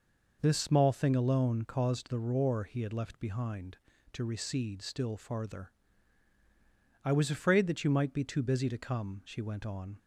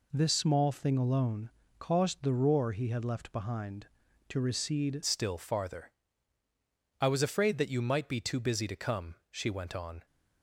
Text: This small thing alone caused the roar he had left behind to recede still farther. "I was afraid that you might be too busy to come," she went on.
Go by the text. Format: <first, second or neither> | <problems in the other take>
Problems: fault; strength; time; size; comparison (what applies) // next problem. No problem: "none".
first | pauses between "alone" and "caused"; slight; at 1.4 s; 0.28 s long // changes voice at "still"; from 5.0 s on; 5.0 s long